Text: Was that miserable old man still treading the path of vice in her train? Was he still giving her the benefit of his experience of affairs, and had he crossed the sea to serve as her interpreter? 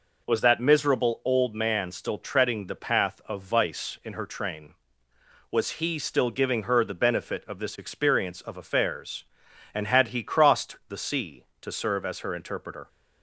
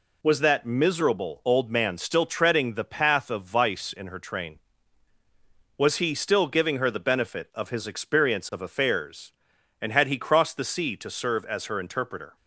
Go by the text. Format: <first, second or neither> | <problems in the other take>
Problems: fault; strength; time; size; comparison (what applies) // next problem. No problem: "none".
second | says "this" for "his"; at 7.5 s